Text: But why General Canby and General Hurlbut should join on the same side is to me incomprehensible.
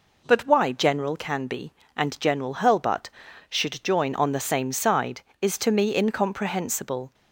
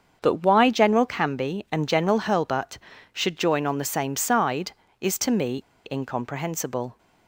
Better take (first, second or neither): first